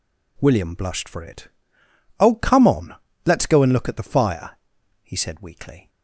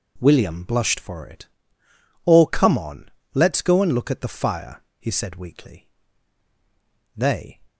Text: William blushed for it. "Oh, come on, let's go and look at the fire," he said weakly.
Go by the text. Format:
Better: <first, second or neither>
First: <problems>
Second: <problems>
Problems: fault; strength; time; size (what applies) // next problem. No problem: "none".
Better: first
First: none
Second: goes on to say "They"; slight; from 7.1 s on; 0.46 s long